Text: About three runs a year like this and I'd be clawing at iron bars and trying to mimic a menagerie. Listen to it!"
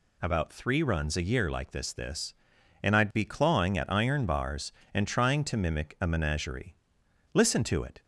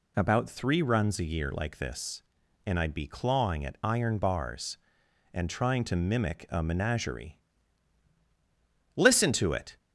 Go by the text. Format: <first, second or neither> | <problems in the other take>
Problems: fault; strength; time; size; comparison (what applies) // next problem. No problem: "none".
second | says "this" twice; at 1.9 s